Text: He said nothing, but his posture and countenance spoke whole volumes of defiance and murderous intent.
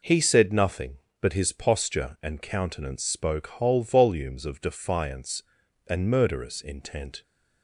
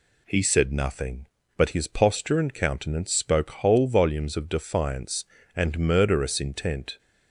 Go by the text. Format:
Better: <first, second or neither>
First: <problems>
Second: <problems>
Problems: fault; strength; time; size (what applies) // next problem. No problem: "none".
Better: neither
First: none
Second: none